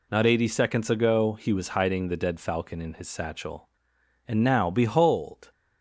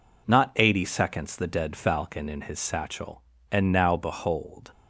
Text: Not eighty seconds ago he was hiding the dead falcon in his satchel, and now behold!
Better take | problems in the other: first | skips "ago he was hiding"; at 1.3 s

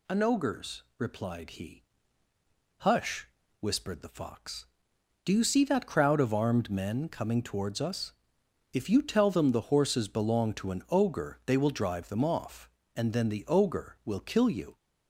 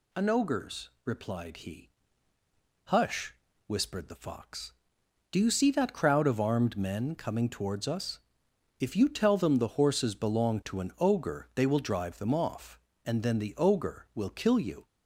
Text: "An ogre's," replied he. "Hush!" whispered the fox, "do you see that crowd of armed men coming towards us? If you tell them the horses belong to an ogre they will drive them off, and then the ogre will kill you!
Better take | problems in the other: neither | none

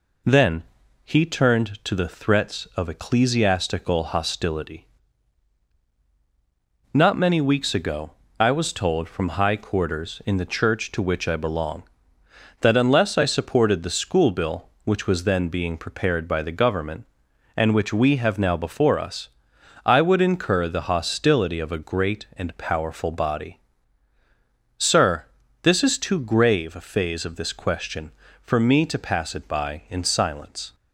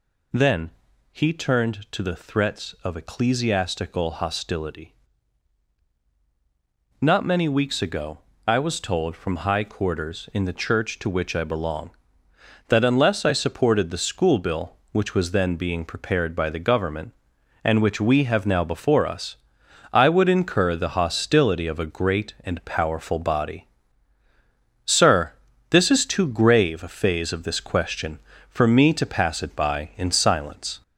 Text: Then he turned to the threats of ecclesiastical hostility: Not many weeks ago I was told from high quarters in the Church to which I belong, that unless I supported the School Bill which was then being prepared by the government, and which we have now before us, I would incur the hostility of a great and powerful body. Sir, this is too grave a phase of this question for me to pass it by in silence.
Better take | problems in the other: first | gets louder; throughout; 3.5 dB // pauses between "Then" and "he"; at 0.6 s; 0.42 s long; also in the first // pauses between "ago" and "I"; slight; at 8.1 s; 0.28 s long; slight in the first

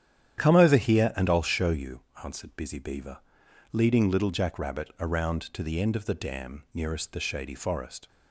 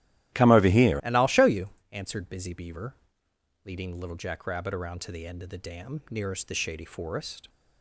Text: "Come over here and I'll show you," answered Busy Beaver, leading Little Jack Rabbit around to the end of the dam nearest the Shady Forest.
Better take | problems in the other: first | starts louder than the rest; strong; until 1.3 s; 14 dB; strong in the first // changes voice at "and"; from 1.0 s on; 6.4 s long

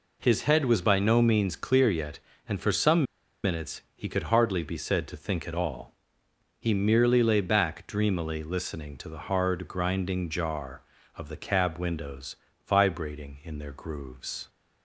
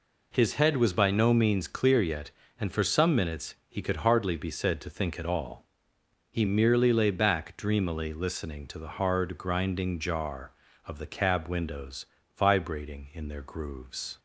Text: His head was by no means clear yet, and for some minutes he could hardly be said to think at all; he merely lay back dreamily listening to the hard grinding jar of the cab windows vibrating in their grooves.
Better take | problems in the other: second | pauses between "some" and "minutes"; at 3.0 s; 0.41 s long // pauses between "windows" and "vibrating"; slight; at 12.3 s; 0.32 s long; slight in the second

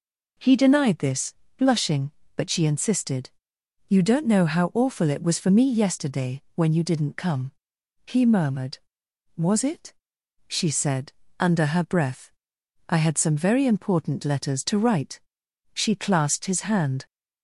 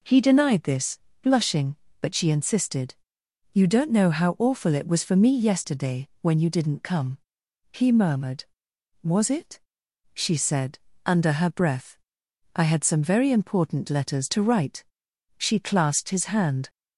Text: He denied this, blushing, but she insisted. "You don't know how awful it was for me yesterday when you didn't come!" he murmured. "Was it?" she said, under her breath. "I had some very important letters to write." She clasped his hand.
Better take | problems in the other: neither | none

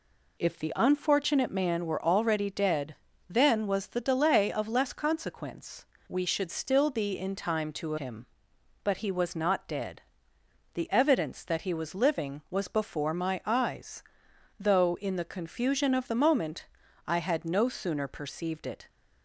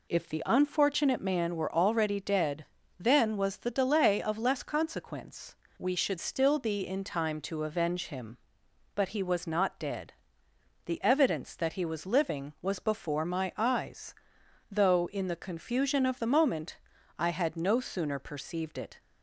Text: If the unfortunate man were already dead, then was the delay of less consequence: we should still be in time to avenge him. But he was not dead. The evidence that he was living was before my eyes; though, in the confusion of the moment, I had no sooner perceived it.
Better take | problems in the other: second | skips "avenge"; at 7.9 s

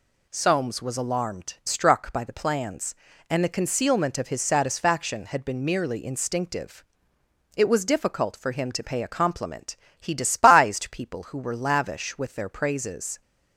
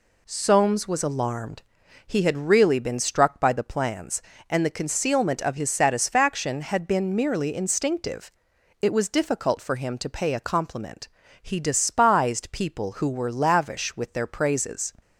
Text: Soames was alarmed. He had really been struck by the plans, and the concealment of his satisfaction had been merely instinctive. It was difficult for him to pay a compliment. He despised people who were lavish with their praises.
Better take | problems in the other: second | skips "He had really been"; at 1.6 s

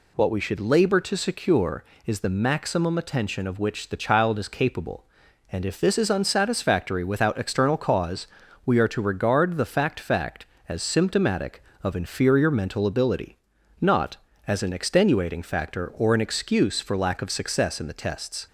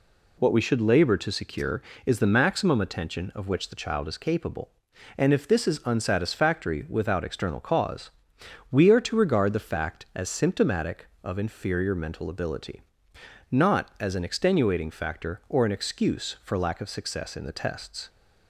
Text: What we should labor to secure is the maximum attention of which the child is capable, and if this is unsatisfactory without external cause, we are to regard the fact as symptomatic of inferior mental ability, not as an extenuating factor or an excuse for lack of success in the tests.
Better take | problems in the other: second | says "fact" twice; at 9.9 s

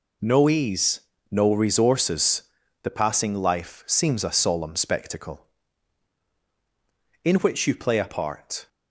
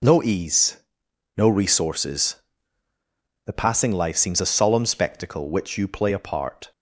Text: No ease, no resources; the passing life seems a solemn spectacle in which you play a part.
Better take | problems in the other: first | skips "in"; at 5.4 s

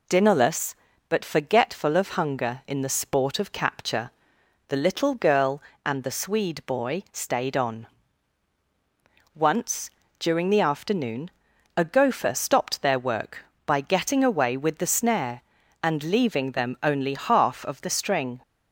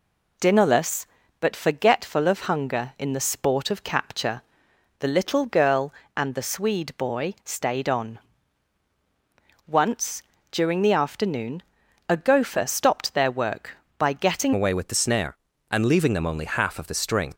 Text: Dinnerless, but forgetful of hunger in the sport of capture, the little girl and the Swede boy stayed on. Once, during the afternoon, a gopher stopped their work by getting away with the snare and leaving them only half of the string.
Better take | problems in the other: first | changes voice at "away"; from 14.5 s on; 2.8 s long

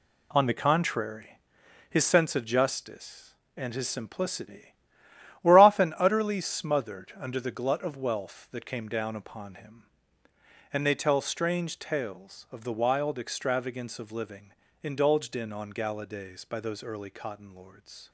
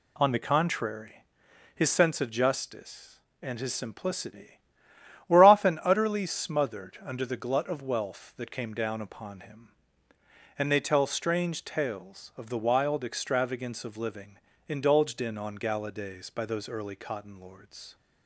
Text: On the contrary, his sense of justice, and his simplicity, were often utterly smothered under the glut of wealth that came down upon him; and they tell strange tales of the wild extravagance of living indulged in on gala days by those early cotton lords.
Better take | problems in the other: second | gets quieter; strong; throughout; 7.5 dB // pauses between "living" and "indulged"; slight; at 14.5 s; 0.28 s long; slight in the second

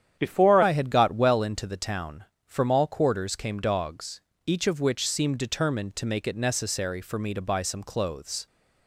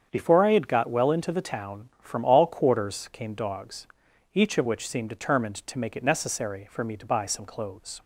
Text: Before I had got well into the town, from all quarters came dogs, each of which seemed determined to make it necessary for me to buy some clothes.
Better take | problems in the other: second | starts louder than the rest; strong; until 1.2 s; 9 dB; strong in the second // changes voice at "I"; from 0.6 s on; 7.8 s long

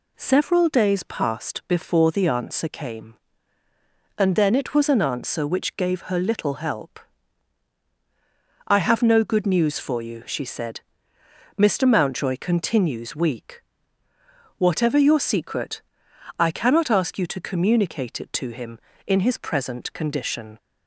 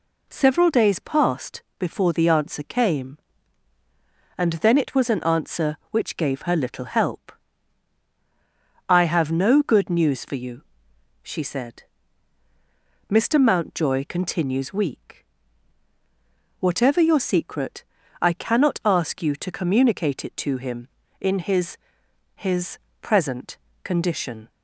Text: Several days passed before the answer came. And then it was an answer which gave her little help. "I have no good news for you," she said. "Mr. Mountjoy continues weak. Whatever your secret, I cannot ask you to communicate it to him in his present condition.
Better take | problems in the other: first | pauses between "passed" and "before"; slight; at 1.6 s; 0.18 s long // says "his" twice; at 22.3 s // pauses between "present" and "condition"; slight; at 23.5 s; 0.24 s long

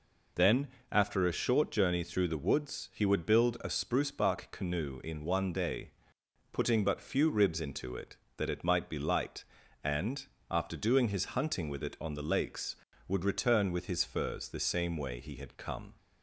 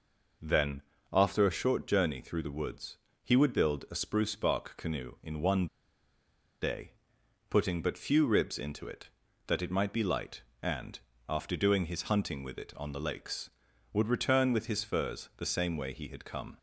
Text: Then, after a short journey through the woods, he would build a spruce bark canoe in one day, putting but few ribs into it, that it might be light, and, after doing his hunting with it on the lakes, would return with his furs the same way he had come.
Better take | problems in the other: first | pauses between "one" and "day"; noticeable; at 5.6 s; 0.94 s long

